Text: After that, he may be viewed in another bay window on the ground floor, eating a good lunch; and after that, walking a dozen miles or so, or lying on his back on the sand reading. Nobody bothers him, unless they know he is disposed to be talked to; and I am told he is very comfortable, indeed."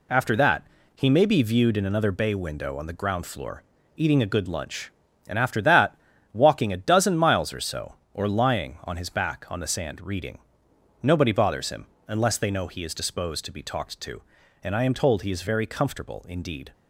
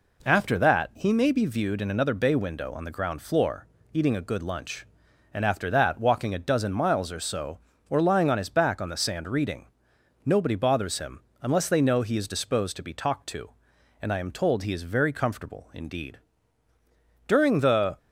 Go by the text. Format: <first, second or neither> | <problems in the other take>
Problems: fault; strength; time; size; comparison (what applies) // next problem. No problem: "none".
first | goes on to say "During the"; noticeable; from 17.2 s on; 0.70 s long